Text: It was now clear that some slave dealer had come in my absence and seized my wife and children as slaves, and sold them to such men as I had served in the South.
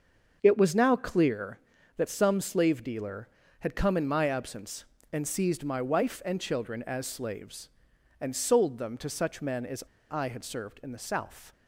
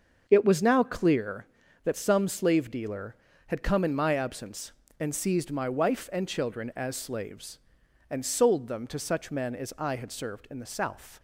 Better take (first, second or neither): second